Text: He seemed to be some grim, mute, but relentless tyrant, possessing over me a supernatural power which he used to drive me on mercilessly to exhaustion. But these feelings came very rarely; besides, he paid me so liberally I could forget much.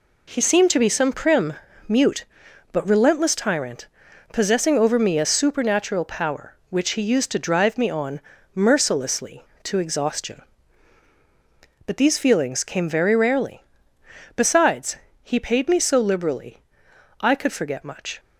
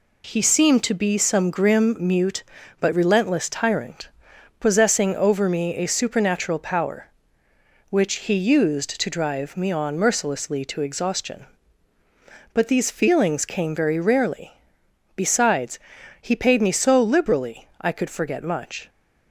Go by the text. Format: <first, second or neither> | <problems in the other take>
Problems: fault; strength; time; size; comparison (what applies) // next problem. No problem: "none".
second | says "prim" for "grim"; at 1.1 s // pauses between "on" and "mercilessly"; slight; at 8.1 s; 0.34 s long // pauses between "liberally" and "I"; noticeable; at 16.6 s; 0.60 s long